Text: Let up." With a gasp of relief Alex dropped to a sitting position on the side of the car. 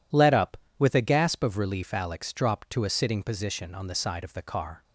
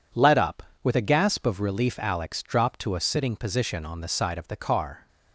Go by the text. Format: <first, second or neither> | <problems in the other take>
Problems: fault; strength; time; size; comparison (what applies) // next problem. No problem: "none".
neither | none